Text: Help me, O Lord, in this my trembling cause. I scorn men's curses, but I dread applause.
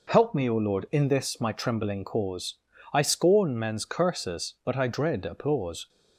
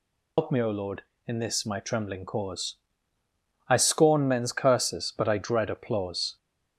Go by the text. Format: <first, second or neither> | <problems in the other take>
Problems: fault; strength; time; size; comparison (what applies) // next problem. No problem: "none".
first | loses the start of "Help"; at 0.3 s; 110 ms